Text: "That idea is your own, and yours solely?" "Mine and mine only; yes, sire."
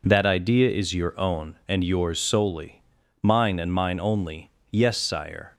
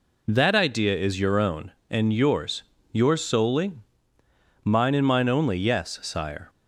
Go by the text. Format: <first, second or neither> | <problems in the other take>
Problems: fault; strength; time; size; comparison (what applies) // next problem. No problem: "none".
first | says "yours" twice; at 2.9 s